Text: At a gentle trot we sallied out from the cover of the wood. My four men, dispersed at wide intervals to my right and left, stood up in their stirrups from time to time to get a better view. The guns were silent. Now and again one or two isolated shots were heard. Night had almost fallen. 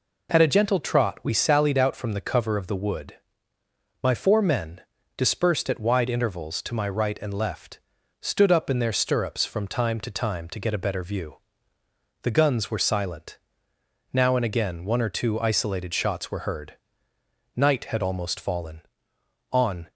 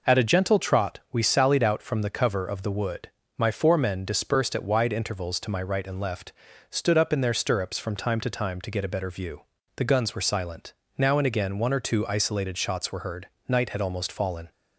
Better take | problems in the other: second | goes on to say "On"; slight; from 19.5 s on; 0.40 s long

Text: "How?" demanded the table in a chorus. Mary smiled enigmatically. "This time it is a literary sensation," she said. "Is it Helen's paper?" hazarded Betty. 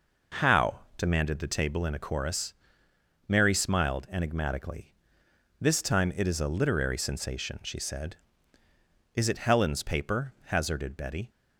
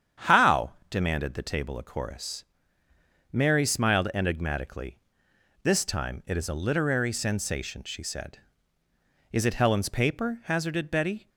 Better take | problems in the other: first | starts louder than the rest; strong; until 1.4 s; 8.5 dB // skips "in"; at 1.7 s

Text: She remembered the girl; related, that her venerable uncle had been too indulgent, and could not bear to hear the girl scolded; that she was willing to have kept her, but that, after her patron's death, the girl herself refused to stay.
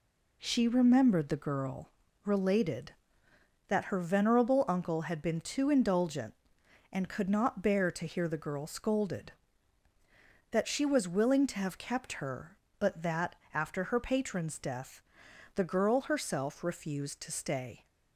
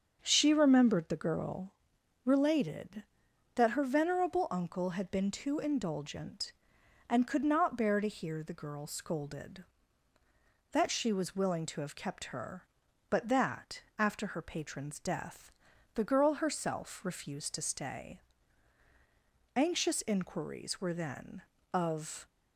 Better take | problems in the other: first | starts louder than the rest; until 1.2 s; 7 dB // goes on to say "Anxious inquiries were then of"; strong; from 19.5 s on; 2.7 s long

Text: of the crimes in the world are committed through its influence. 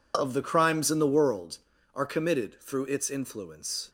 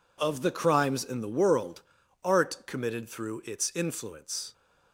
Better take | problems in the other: first | says "art" for "are"; at 2.2 s

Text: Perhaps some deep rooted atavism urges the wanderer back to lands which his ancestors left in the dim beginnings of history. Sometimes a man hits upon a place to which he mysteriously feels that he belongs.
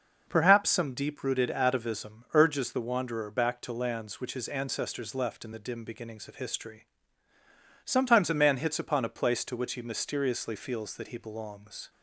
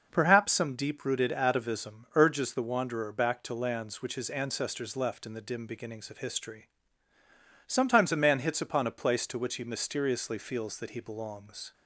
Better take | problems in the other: neither | none

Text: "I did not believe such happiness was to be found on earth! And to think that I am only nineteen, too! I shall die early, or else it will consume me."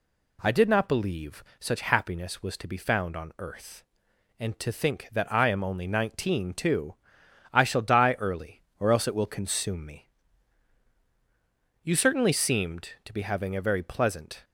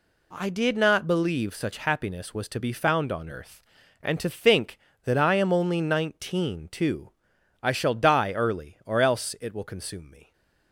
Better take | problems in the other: second | goes on to say "You certainly seemed to be having a very pleasant"; strong; from 11.8 s on; 2.6 s long

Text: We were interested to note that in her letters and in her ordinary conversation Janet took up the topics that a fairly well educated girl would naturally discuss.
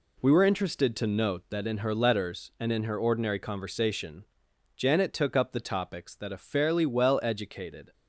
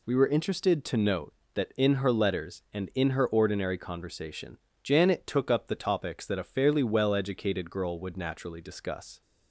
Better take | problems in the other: second | pauses between "conversation" and "Janet"; noticeable; at 4.2 s; 0.52 s long; slight in the second // stops before "girl would naturally discuss"; at 7.9 s

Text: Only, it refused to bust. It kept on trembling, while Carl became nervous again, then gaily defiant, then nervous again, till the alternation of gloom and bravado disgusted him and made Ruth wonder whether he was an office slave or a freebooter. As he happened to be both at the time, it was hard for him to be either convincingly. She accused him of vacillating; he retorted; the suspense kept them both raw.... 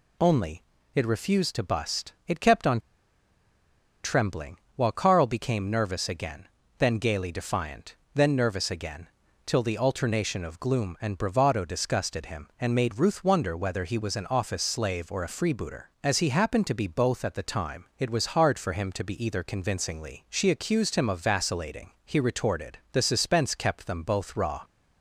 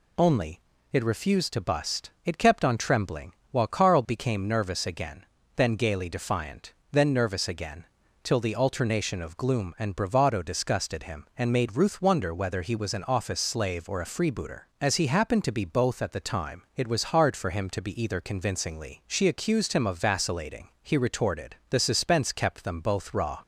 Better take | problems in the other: second | pauses between "on" and "trembling"; at 2.7 s; 1.2 s long

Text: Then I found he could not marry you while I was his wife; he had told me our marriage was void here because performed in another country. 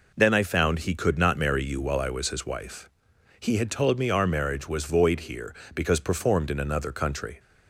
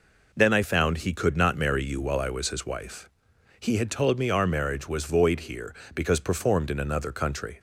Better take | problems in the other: neither | none

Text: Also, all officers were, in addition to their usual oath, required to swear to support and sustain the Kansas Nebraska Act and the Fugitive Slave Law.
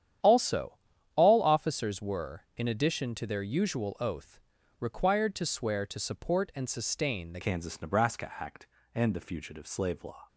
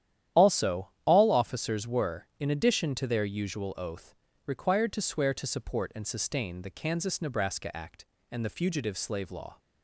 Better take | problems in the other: second | starts louder than the rest; strong; until 1.6 s; 10 dB; strong in the second // changes voice at "Kansas"; from 7.4 s on; 2.8 s long

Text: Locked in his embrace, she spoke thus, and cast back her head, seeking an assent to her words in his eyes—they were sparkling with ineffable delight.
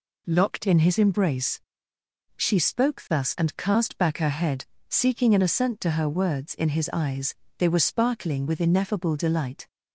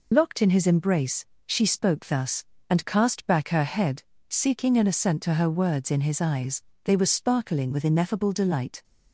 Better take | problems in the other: first | loses the start of "Locked"; at 0.1 s; 60 ms

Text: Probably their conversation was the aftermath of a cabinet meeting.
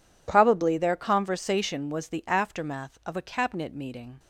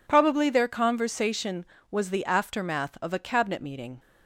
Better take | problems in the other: neither | none

